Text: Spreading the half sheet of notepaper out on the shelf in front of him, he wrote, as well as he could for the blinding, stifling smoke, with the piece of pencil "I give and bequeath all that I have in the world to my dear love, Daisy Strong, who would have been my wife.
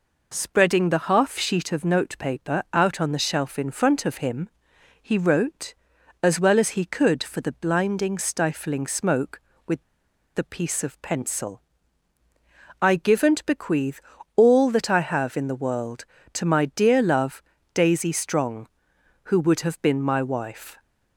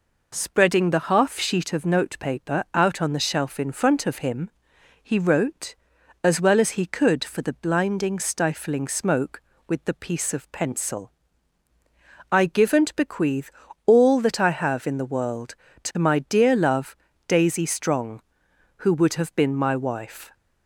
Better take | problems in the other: second | pauses between "with" and "the"; noticeable; at 9.8 s; 0.51 s long // pauses between "pencil" and "I"; at 11.6 s; 1.2 s long; also in the second // pauses between "bequeath" and "all"; slight; at 14.0 s; 0.34 s long; slight in the second

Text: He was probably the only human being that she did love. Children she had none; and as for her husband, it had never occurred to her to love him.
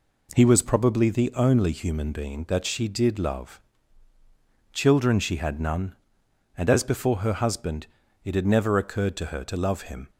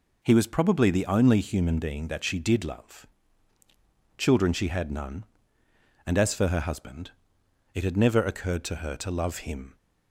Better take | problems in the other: second | says "before" for "for"; at 6.8 s

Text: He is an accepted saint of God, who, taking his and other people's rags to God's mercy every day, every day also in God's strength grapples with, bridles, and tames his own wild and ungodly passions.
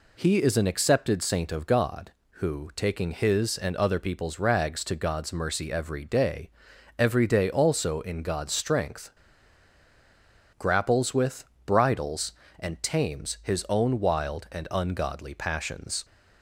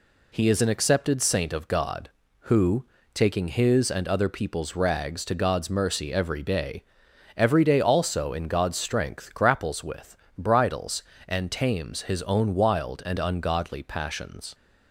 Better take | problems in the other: second | pauses between "strength" and "grapples"; strong; at 9.1 s; 1.4 s long

